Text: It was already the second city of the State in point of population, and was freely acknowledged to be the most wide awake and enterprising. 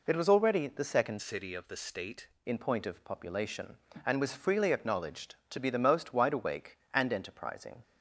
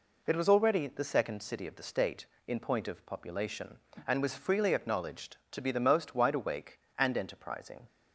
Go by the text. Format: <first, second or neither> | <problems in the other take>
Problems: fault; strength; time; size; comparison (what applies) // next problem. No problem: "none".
second | changes voice from "city" to "State"; from 1.2 to 2.2 s; 1.0 s long